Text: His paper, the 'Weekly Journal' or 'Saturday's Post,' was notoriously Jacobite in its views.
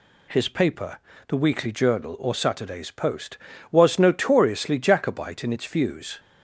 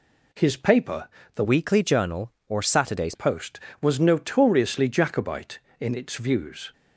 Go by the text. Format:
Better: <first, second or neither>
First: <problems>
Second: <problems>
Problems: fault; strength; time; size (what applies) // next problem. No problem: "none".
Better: first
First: none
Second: changes voice from "Weekly" to "Saturday's"; from 1.4 to 3.1 s; 1.7 s long